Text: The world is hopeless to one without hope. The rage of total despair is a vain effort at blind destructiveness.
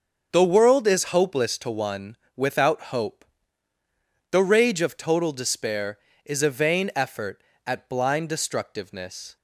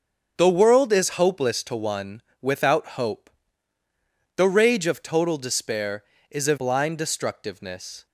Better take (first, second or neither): first